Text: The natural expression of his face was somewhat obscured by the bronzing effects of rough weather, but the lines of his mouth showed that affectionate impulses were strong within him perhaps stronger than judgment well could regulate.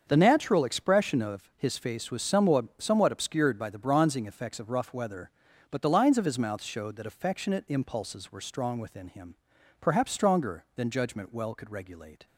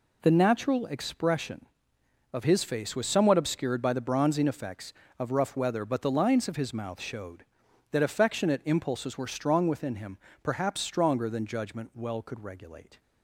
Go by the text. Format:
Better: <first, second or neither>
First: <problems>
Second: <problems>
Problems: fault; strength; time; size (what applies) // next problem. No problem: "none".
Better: second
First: starts louder than the rest; until 1.0 s; 7 dB // says "somewhat" twice; at 2.7 s // pauses between "him" and "perhaps"; noticeable; at 9.3 s; 0.46 s long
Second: pauses between "him" and "perhaps"; slight; at 10.1 s; 0.24 s long